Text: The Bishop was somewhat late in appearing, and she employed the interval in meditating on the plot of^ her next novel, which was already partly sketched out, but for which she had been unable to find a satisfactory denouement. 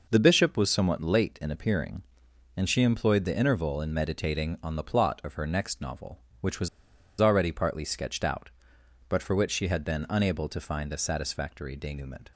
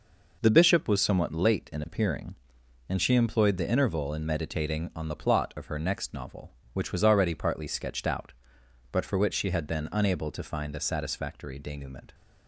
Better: second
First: pauses between "was" and "already"; noticeable; at 6.6 s; 0.52 s long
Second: none

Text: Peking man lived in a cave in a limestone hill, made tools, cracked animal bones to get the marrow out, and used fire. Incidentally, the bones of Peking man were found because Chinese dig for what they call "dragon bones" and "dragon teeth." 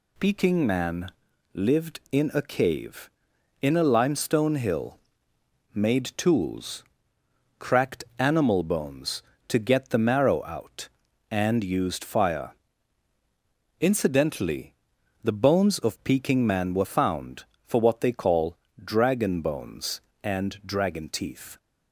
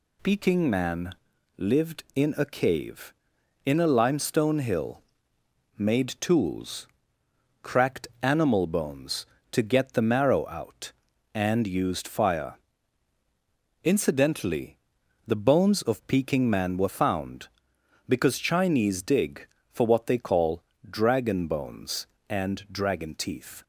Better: second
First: pauses between "man" and "lived"; at 1.0 s; 0.44 s long // skips "because Chinese dig"; at 17.5 s // pauses between "call" and "dragon"; slight; at 18.5 s; 0.22 s long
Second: pauses between "man" and "lived"; at 1.1 s; 0.44 s long // pauses between "call" and "dragon"; slight; at 20.6 s; 0.22 s long

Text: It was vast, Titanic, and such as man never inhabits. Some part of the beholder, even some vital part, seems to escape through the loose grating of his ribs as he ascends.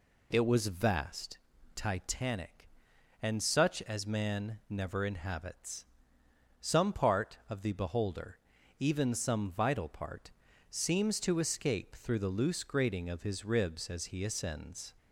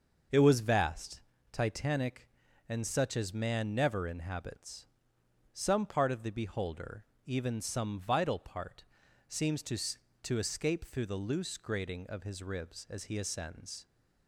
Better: first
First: none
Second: starts louder than the rest; noticeable; until 1.6 s; 6 dB // says "to" twice; at 10.2 s

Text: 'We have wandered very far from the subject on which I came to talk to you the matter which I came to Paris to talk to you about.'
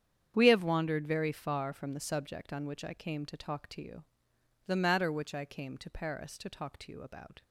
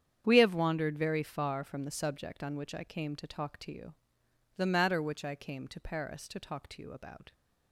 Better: neither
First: starts louder than the rest; strong; until 1.3 s; 8.5 dB // pauses between "you" and "the"; noticeable; at 4.0 s; 0.64 s long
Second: starts louder than the rest; strong; until 1.2 s; 8.5 dB // pauses between "you" and "the"; noticeable; at 3.9 s; 0.64 s long

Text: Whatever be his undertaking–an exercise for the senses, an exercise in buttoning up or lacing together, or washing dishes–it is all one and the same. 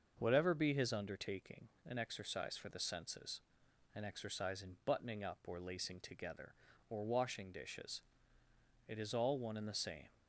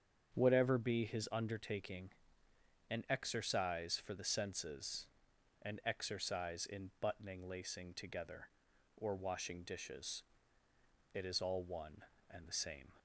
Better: first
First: starts louder than the rest; until 1.2 s; 6 dB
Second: starts louder than the rest; strong; until 1.3 s; 7.5 dB // skips "up or"; at 7.4 s

